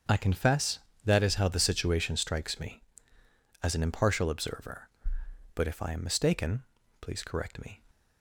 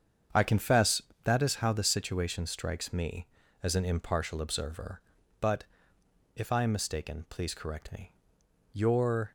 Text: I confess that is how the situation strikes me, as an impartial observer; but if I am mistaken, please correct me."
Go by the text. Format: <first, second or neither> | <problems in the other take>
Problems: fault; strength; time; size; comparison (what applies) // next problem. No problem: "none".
first | starts louder than the rest; strong; until 1.5 s; 7.5 dB; also in the first // pauses between "but" and "if"; noticeable; at 5.6 s; 0.72 s long // goes on to say "Your"; from 8.7 s on; 0.60 s long